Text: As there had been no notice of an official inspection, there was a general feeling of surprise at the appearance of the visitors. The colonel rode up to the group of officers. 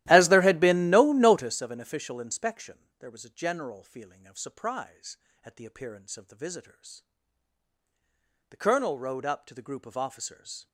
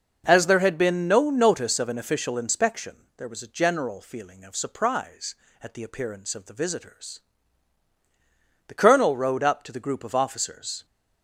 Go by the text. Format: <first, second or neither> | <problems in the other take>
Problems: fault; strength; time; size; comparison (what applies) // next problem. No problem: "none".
second | starts louder than the rest; strong; until 1.5 s; 14.5 dB